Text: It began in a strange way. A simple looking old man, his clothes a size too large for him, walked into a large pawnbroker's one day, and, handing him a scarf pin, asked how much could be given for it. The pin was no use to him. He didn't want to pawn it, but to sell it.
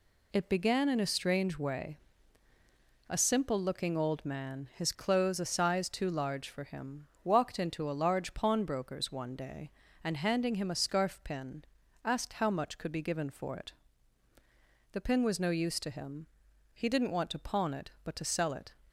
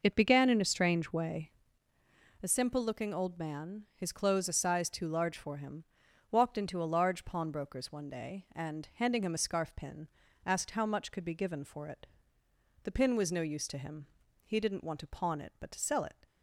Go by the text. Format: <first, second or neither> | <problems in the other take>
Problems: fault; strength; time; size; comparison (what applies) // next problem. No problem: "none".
first | starts louder than the rest; noticeable; until 1.8 s; 5.5 dB